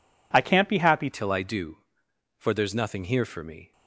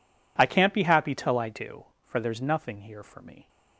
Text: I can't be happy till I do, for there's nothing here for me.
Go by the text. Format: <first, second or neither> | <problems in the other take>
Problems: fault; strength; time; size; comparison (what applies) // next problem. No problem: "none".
second | changes voice at "till"; from 1.1 s on; 2.6 s long